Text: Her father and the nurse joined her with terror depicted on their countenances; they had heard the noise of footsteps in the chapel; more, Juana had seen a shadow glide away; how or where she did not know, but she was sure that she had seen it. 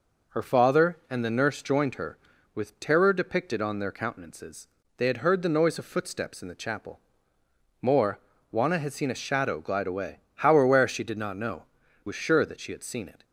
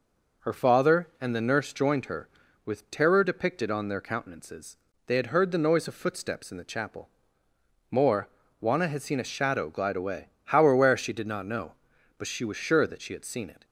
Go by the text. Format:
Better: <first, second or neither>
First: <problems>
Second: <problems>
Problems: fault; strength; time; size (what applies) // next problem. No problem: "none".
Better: second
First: skips "but she"; at 11.8 s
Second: none